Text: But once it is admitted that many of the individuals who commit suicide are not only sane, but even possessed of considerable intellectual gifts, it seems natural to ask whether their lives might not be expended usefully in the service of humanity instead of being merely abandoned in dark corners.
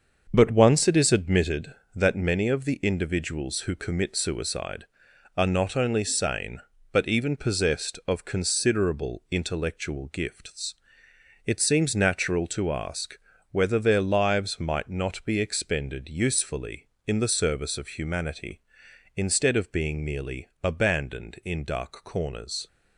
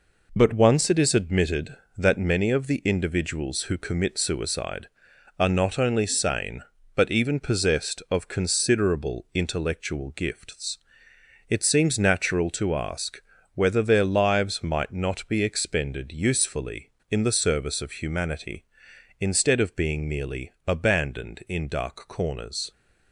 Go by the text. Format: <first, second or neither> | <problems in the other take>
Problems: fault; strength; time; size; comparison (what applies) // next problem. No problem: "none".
second | starts louder than the rest; until 1.5 s; 6.5 dB // pauses between "ask" and "whether"; slight; at 13.1 s; 0.34 s long; slight in the second